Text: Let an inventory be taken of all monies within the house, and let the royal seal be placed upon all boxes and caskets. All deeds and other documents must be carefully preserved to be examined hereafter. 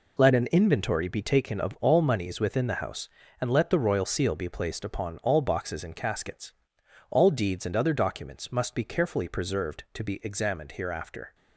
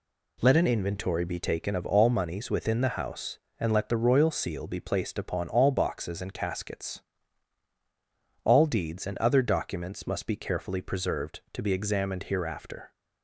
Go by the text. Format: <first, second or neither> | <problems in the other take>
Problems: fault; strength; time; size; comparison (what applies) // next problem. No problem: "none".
neither | none